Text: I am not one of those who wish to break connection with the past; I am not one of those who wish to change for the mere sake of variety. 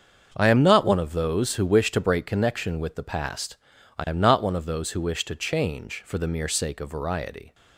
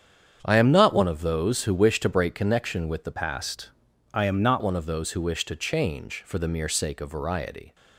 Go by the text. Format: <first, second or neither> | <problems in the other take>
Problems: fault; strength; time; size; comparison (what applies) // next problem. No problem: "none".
first | starts louder than the rest; strong; until 1.4 s; 8 dB; also in the first // changes voice from "past" to "not"; from 3.1 to 4.6 s; 1.5 s long